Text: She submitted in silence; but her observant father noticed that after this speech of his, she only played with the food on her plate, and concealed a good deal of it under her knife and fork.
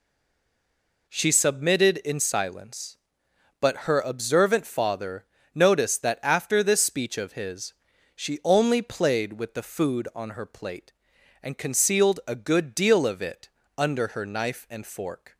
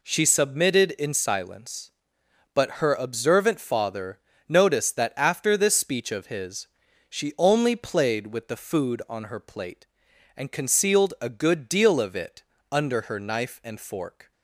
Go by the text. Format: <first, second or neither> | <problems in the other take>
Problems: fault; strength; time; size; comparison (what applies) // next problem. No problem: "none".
second | stays silent before the first word; until 1.0 s; 1.0 s long // pauses between "father" and "noticed"; slight; at 5.2 s; 0.28 s long; slight in the second // pauses between "it" and "under"; slight; at 13.4 s; 0.28 s long; slight in the second